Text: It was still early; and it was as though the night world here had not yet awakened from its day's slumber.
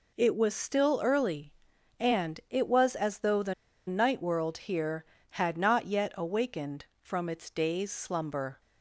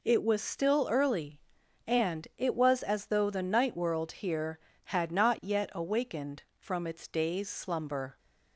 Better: second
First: pauses between "the" and "night"; slight; at 3.5 s; 0.34 s long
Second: none

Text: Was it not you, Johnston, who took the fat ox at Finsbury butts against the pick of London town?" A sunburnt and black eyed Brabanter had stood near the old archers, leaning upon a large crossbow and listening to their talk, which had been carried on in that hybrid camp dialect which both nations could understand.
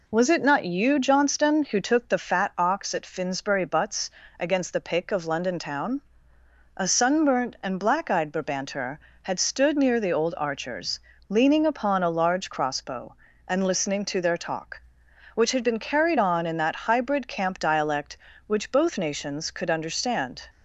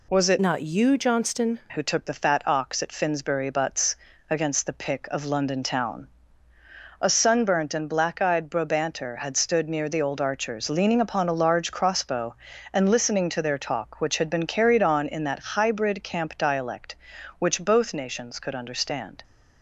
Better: first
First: pauses between "butts" and "against"; slight; at 4.0 s; 0.30 s long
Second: changes voice from "not" to "Johnston"; from 0.4 to 1.6 s; 1.2 s long // pauses between "butts" and "against"; slight; at 3.9 s; 0.34 s long

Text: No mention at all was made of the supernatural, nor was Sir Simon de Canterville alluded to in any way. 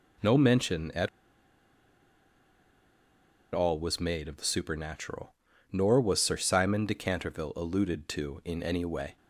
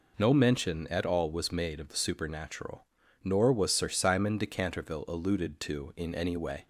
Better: second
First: pauses between "at" and "all"; strong; at 1.0 s; 2.4 s long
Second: none

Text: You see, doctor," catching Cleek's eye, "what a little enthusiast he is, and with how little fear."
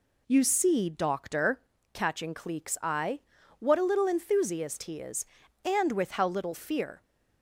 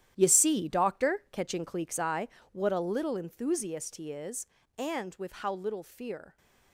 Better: first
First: none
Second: gets quieter; strong; throughout; 12.5 dB

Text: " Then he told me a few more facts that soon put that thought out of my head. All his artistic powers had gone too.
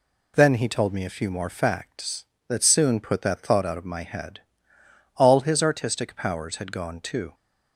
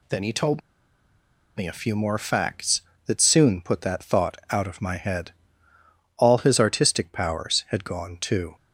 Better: first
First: none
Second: pauses between "told" and "me"; noticeable; at 0.5 s; 0.96 s long // pauses between "thought" and "out"; slight; at 4.3 s; 0.16 s long

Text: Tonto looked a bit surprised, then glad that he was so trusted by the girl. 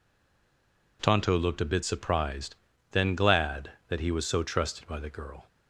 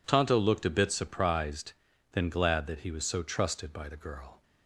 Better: second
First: stays silent before the first word; until 0.9 s; 0.9 s long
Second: none

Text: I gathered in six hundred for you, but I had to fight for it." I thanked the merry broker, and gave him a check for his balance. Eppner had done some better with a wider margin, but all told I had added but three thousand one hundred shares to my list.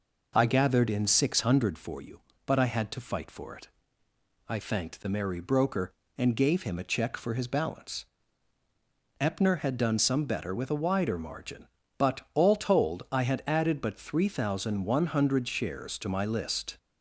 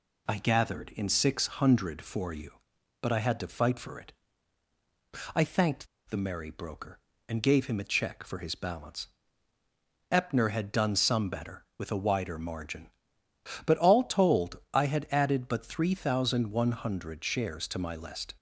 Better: first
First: none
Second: pauses between "thanked" and "the"; slight; at 5.8 s; 0.21 s long

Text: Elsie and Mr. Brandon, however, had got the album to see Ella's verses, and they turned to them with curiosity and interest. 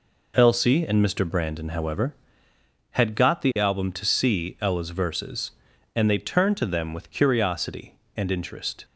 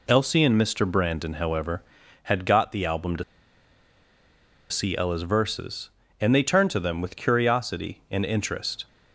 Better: first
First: none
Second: pauses between "to" and "see"; strong; at 3.2 s; 1.4 s long

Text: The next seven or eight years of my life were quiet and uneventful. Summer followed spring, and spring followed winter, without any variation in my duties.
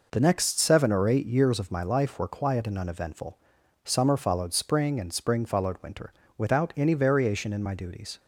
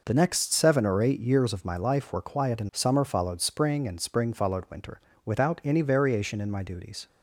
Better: first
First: none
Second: skips "uneventful"; at 2.7 s

